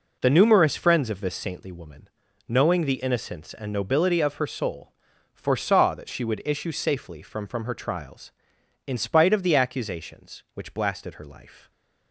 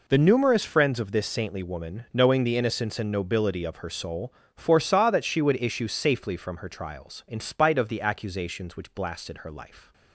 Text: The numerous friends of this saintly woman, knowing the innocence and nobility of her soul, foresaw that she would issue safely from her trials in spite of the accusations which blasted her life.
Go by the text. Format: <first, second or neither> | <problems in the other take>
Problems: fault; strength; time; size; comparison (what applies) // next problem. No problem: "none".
second | says "from" twice; at 7.4 s